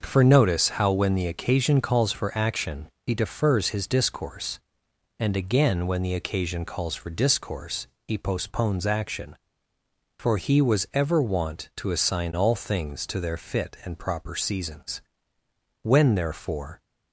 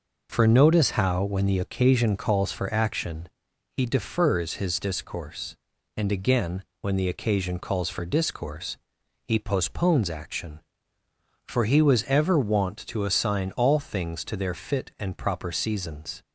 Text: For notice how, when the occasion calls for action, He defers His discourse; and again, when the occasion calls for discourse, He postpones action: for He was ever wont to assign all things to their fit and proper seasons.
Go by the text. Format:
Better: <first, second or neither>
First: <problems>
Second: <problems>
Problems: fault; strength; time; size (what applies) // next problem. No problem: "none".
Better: second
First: starts louder than the rest; noticeable; until 1.0 s; 6 dB // goes on to say "When therefore"; noticeable; from 15.8 s on; 0.98 s long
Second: none